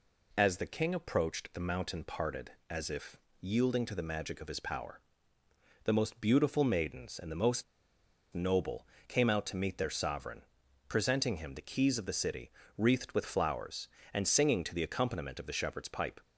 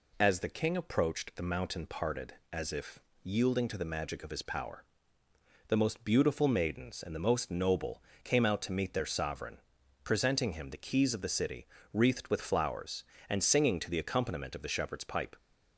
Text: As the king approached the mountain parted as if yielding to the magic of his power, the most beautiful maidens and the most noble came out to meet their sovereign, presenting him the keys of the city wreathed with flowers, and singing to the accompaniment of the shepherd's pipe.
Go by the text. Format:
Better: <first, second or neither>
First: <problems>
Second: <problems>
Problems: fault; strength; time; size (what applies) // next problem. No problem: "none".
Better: second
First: pauses between "if" and "yielding"; slight; at 3.1 s; 0.24 s long // pauses between "most" and "noble"; noticeable; at 7.6 s; 0.69 s long // pauses between "noble" and "came"; slight; at 8.8 s; 0.22 s long // pauses between "city" and "wreathed"; slight; at 12.4 s; 0.26 s long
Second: pauses between "if" and "yielding"; slight; at 3.0 s; 0.24 s long // pauses between "noble" and "came"; slight; at 8.0 s; 0.22 s long // pauses between "city" and "wreathed"; slight; at 11.6 s; 0.26 s long